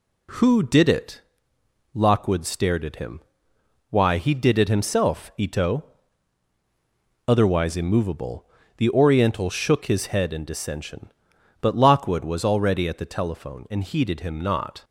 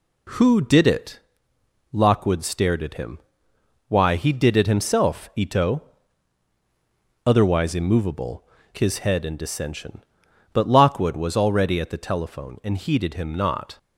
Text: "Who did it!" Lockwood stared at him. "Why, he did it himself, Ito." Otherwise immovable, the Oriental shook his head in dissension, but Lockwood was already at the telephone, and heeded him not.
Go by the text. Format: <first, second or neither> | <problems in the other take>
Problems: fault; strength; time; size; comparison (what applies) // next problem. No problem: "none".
first | skips "the Oriental shook"; at 8.6 s